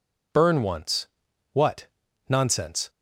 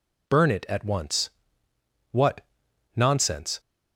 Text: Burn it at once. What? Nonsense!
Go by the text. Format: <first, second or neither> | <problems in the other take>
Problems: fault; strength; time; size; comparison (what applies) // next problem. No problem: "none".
second | skips "it at"; at 0.6 s